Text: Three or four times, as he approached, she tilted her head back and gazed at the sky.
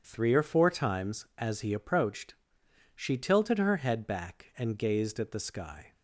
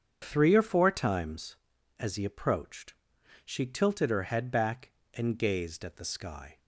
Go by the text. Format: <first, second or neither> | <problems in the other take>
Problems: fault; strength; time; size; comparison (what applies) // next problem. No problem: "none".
neither | starts louder than the rest; strong; the same in both